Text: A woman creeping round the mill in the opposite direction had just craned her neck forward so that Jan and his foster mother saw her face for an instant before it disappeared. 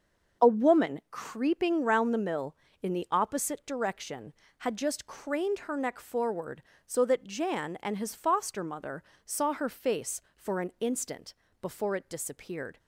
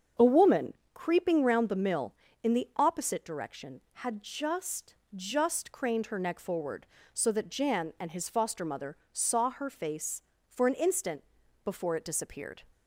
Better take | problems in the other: first | starts louder than the rest; until 1.4 s; 7 dB; also in the first // pauses between "woman" and "creeping"; slight; at 0.7 s; 0.22 s long // says "just" twice; at 5.1 s // pauses between "mother" and "saw"; slight; at 8.9 s; 0.16 s long; slight in the first // pauses between "instant" and "before"; at 11.2 s; 0.40 s long; slight in the first

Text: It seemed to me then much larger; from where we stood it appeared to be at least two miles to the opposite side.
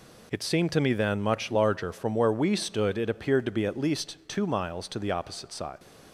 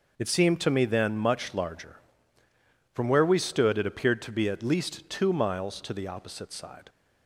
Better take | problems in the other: neither | none

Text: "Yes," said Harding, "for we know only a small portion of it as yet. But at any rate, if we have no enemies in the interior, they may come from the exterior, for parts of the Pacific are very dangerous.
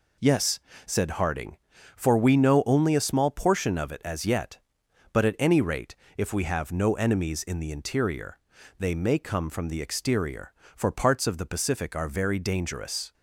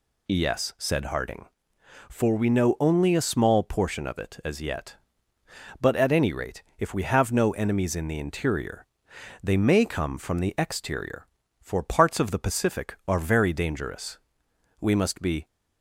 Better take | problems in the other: first | goes on to say "We must be"; noticeable; from 14.8 s on; 0.66 s long

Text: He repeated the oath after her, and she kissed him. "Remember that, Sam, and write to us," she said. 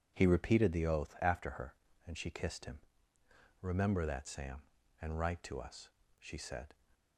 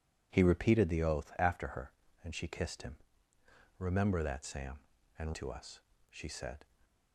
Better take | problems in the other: first | skips "write"; at 5.3 s

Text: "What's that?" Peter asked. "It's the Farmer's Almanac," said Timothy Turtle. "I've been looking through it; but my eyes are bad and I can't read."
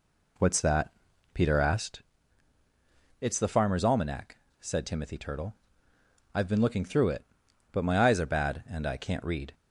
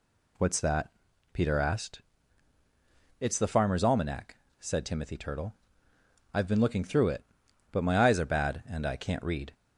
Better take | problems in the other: second | starts louder than the rest; slight; until 2.1 s; 3 dB

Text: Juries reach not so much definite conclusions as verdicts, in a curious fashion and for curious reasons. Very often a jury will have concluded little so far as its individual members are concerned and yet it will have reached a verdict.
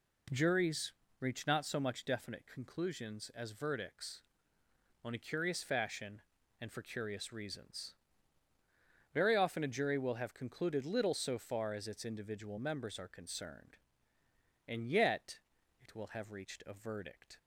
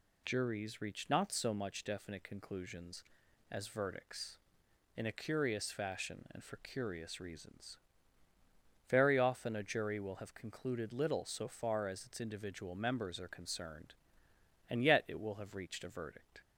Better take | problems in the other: second | pauses between "Juries" and "reach"; slight; at 0.9 s; 0.28 s long // says "on" for "in"; at 5.0 s // pauses between "yet" and "it"; at 15.3 s; 0.42 s long

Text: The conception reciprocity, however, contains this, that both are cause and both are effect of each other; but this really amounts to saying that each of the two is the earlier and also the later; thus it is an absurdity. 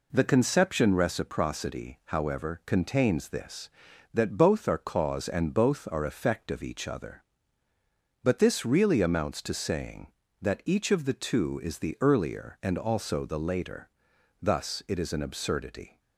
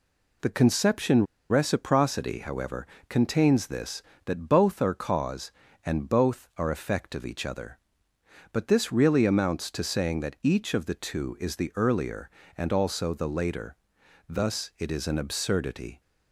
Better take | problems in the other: first | pauses between "conception" and "reciprocity"; slight; at 1.2 s; 0.24 s long

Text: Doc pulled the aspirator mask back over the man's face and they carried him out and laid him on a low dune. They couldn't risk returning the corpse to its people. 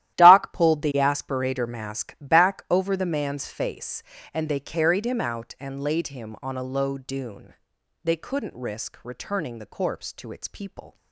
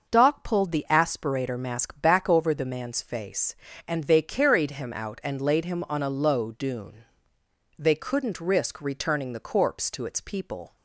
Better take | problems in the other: second | gets quieter; strong; throughout; 14.5 dB // starts louder than the rest; strong; until 1.1 s; 13.5 dB; also in the second

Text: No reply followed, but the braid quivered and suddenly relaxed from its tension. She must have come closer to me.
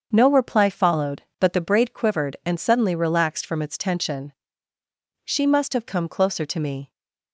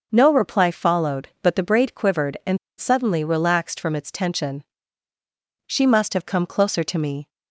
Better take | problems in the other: first | starts louder than the rest; until 1.1 s; 6 dB; also in the first // pauses between "and" and "suddenly"; slight; at 2.5 s; 0.22 s long

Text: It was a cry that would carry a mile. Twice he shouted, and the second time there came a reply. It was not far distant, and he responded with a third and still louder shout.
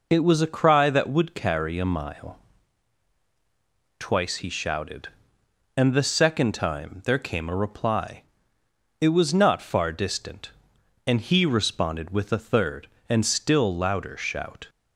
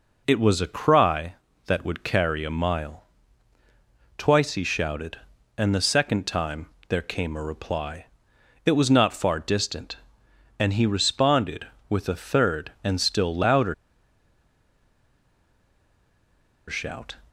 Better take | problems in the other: first | pauses between "time" and "there"; slight; at 6.6 s; 0.24 s long // pauses between "louder" and "shout"; strong; at 13.7 s; 2.9 s long

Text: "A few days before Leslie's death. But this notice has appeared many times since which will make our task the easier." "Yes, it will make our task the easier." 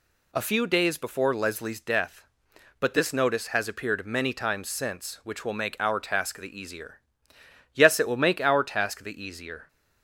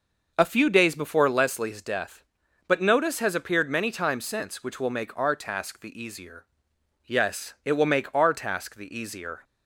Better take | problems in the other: first | skips "this"; at 2.8 s

